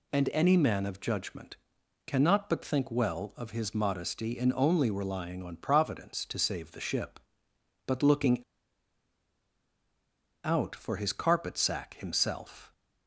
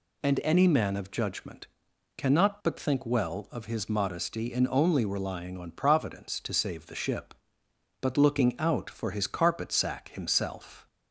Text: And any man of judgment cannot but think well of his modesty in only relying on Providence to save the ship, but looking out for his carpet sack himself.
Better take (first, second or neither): second